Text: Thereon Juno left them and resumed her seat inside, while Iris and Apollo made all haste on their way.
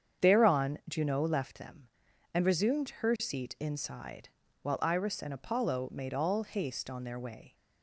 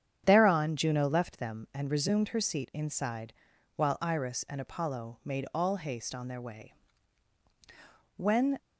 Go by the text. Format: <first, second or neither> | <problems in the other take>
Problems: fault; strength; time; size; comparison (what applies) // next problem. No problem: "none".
first | starts louder than the rest; strong; until 1.2 s; 8.5 dB; strong in the first // goes on to say "When"; slight; from 8.1 s on; 0.42 s long